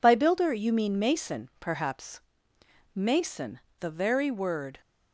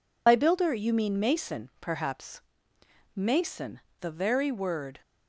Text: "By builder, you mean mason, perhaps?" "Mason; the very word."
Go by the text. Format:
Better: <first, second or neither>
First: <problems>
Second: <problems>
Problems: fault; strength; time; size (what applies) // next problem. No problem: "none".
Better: first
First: none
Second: loses the start of "By"; at 0.2 s; 35 ms